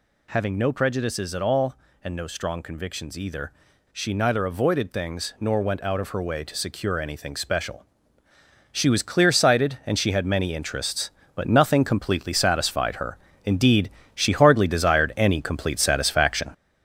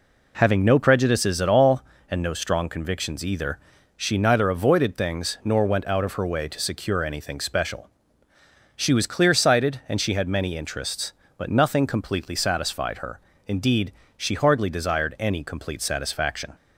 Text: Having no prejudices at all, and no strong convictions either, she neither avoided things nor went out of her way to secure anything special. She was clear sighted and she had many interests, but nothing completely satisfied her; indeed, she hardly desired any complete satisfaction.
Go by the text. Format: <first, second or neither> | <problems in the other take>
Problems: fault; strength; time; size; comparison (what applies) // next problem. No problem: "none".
second | gets louder; throughout; 6 dB